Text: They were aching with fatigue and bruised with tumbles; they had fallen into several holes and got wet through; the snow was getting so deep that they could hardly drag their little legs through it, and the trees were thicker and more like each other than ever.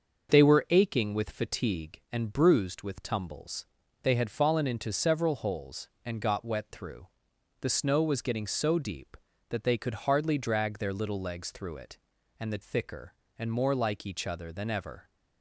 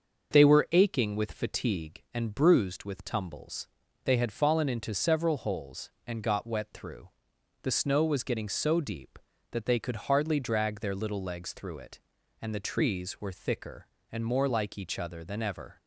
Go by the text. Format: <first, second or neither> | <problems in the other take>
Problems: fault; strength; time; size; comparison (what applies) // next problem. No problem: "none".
second | starts louder than the rest; until 1.3 s; 6 dB; also in the second // skips "trees were"; at 12.6 s